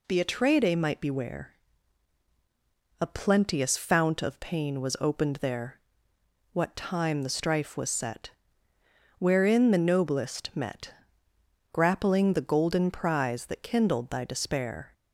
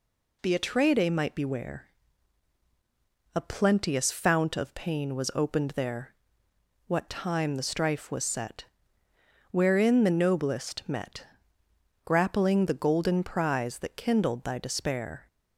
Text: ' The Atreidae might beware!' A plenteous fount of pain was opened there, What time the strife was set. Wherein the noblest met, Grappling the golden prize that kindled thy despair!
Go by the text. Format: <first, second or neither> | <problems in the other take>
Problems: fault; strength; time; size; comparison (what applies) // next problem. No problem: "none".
neither | none